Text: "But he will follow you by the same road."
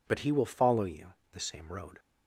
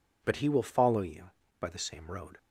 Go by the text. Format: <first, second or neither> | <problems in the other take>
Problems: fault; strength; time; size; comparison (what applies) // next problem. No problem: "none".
second | skips "by"; at 1.2 s